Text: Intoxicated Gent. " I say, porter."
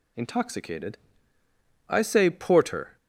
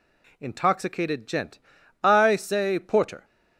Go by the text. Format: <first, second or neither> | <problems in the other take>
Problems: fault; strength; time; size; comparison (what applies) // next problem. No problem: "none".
second | skips "Gent"; at 1.2 s